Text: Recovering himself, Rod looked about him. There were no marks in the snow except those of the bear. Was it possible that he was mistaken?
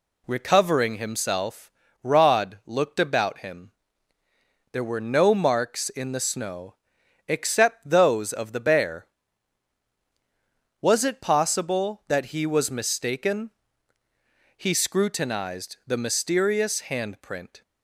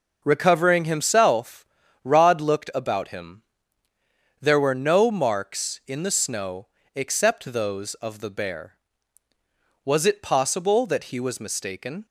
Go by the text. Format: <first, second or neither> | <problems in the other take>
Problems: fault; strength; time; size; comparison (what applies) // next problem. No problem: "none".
second | pauses between "snow" and "except"; noticeable; at 6.7 s; 0.52 s long; slight in the second // goes on to say "He scrutinized the mysterious handprint"; strong; from 14.5 s on; 3.0 s long